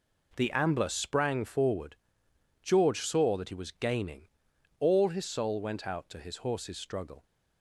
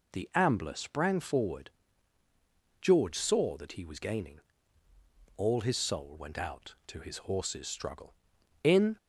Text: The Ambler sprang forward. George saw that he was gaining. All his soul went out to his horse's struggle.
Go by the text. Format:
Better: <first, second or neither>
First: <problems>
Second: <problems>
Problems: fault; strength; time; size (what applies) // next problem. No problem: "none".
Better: first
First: none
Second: goes on to say "In"; slight; from 8.6 s on; 0.34 s long